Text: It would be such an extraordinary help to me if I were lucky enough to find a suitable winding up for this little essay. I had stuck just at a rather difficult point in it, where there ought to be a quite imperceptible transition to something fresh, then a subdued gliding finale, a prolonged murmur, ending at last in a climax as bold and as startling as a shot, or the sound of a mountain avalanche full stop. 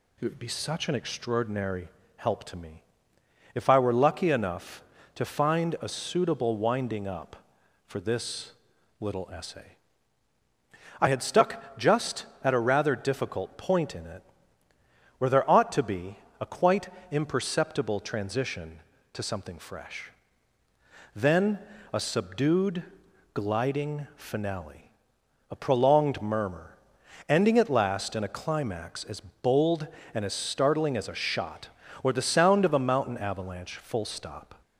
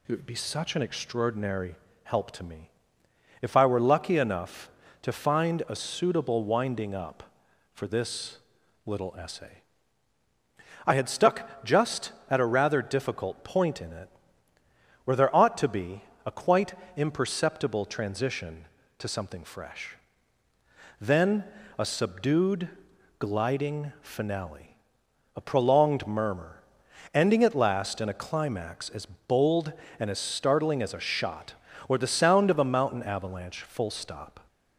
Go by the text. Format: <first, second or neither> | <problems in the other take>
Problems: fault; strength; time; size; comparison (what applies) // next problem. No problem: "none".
neither | pauses between "extraordinary" and "help"; slight; the same in both // pauses between "me" and "if"; noticeable; the same in both // pauses between "this" and "little"; noticeable; the same in both // pauses between "be" and "a"; slight; the same in both // pauses between "quite" and "imperceptible"; slight; the same in both // pauses between "then" and "a"; slight; the same in both // pauses between "subdued" and "gliding"; noticeable; the same in both